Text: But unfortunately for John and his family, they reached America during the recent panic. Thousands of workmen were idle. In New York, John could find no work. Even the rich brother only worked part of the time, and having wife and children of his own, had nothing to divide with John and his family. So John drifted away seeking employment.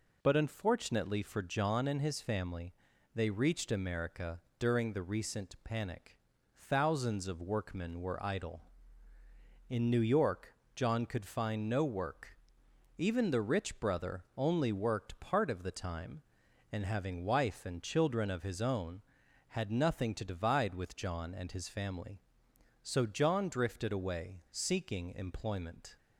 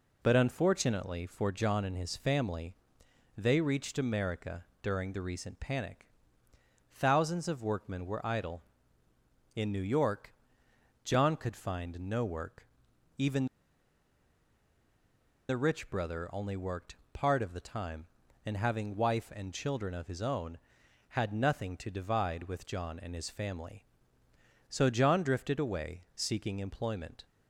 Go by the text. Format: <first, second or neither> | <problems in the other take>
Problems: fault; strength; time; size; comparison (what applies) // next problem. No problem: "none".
first | pauses between "America" and "during"; slight; at 4.6 s; 0.18 s long; slight in the first // pauses between "Even" and "the"; strong; at 13.4 s; 2.0 s long // pauses between "worked" and "part"; slight; at 16.9 s; 0.18 s long